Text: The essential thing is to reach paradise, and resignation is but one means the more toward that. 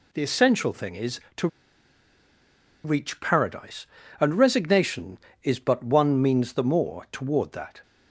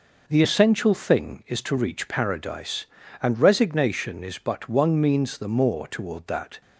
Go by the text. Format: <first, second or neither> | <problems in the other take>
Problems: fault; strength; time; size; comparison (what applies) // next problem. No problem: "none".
second | pauses between "to" and "reach"; strong; at 1.4 s; 1.3 s long